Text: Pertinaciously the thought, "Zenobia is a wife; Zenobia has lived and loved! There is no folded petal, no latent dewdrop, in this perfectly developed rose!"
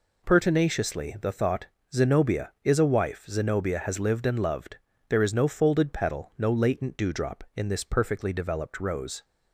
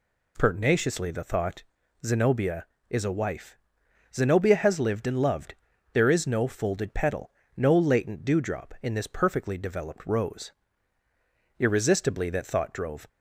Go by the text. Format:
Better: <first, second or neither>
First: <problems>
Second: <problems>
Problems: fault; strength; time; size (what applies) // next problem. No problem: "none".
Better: first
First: none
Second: goes on to say "irresistibly that thought drove"; from 11.5 s on; 1.5 s long